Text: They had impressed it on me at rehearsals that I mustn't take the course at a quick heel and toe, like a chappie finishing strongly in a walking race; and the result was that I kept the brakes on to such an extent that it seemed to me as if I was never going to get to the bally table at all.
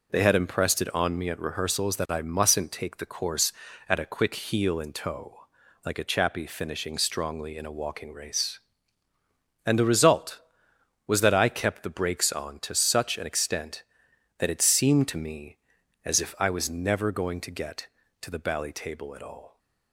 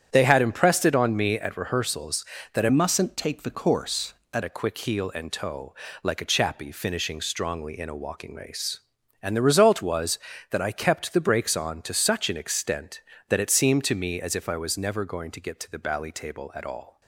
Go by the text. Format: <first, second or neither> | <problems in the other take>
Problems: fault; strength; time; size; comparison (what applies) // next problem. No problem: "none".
first | starts louder than the rest; strong; until 1.1 s; 9 dB // changes voice from "mustn't" to "at"; from 2.6 to 4.4 s; 1.8 s long